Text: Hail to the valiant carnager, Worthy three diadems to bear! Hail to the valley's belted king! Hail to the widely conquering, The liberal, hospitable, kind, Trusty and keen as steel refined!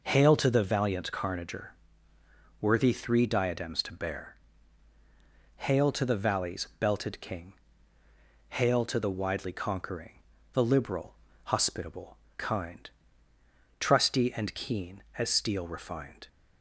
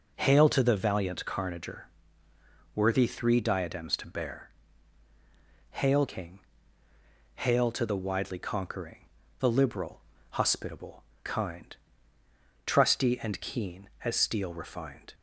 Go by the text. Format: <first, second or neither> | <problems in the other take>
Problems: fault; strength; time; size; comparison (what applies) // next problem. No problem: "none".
first | skips "to the valley's belted"; at 6.0 s